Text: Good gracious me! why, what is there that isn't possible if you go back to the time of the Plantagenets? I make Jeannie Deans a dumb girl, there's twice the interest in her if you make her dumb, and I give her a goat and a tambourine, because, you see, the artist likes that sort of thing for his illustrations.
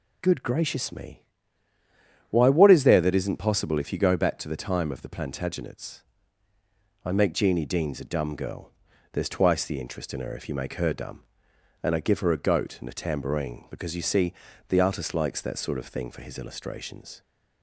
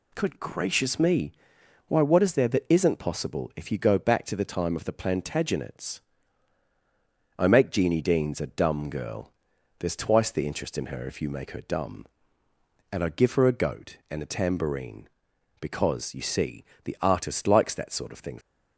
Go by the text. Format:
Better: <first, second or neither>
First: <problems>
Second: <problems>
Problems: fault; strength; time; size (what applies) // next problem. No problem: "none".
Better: first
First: none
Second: stops before "for his illustrations"; at 18.4 s